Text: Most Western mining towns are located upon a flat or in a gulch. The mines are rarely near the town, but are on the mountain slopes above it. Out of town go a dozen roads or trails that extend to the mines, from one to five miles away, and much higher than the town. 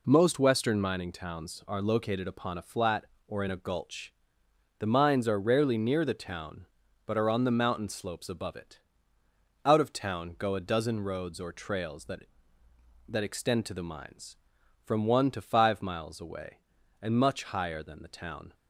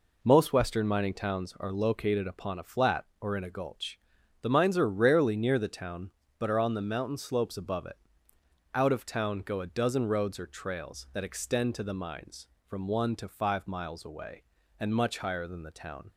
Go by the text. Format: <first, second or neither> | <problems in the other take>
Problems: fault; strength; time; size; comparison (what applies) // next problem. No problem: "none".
second | says "that" twice; at 13.0 s